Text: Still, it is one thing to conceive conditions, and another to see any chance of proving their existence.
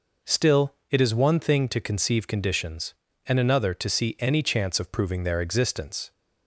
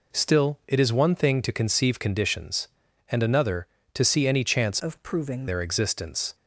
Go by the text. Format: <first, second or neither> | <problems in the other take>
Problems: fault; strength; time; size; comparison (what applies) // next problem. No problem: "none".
first | changes voice from "of" to "proving"; from 4.7 to 5.4 s; 0.7 s long